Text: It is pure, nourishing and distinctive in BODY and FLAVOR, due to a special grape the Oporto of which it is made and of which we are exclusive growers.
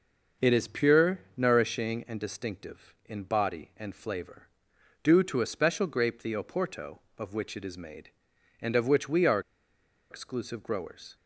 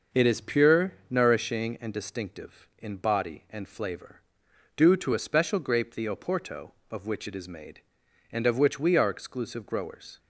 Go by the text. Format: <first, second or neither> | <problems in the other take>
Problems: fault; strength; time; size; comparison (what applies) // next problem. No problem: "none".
second | pauses between "are" and "exclusive"; noticeable; at 9.3 s; 0.70 s long